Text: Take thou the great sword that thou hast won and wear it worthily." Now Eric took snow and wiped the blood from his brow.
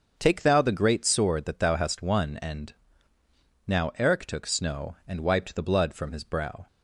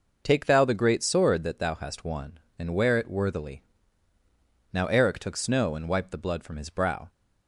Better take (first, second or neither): second